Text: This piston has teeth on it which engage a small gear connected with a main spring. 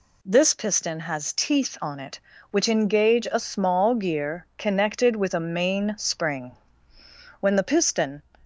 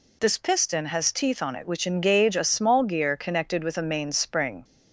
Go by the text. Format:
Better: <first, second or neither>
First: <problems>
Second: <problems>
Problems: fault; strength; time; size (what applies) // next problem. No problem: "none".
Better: second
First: goes on to say "When the piston"; noticeable; from 7.3 s on; 0.82 s long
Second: none